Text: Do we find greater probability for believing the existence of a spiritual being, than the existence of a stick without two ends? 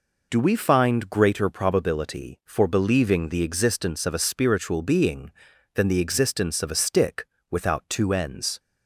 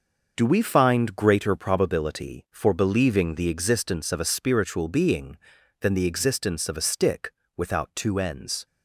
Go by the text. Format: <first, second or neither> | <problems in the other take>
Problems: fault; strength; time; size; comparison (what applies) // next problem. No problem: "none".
first | gets quieter; throughout; 6 dB // pauses between "stick" and "without"; slight; at 7.3 s; 0.26 s long; slight in the first